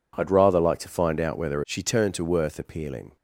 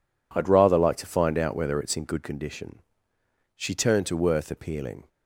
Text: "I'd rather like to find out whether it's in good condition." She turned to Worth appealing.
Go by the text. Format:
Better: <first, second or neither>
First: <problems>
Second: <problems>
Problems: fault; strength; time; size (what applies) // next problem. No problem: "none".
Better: second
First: skips "it's in good condition"; at 1.6 s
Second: none